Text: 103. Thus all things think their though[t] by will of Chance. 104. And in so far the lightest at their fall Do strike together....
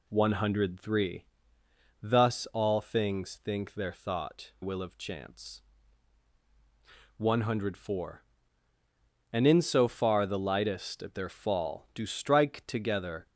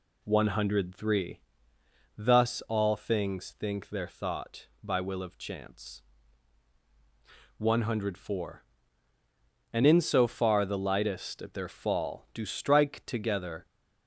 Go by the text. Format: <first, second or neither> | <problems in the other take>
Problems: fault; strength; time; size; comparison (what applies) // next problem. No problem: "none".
second | skips "by"; at 4.5 s